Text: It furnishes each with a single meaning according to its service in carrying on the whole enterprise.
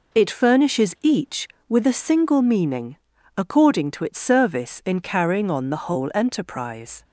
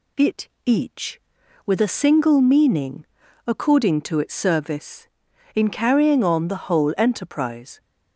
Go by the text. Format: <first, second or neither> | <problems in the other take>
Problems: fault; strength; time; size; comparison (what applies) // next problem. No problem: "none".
first | skips "furnishes"; at 0.5 s // pauses between "meaning" and "according"; at 3.0 s; 0.40 s long; also in the first